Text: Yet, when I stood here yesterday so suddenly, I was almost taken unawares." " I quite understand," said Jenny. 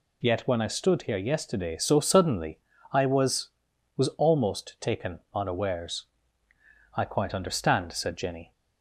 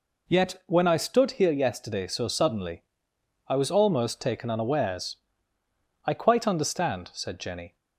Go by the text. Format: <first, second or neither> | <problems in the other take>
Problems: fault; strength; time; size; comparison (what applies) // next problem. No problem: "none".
second | says "was" twice; at 3.9 s // pauses between "taken" and "unawares"; slight; at 5.1 s; 0.16 s long